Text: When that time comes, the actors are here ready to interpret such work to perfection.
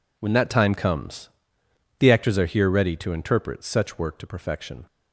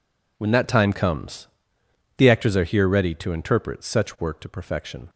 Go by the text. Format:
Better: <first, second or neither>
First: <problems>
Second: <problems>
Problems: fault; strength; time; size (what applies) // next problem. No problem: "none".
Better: neither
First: none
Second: none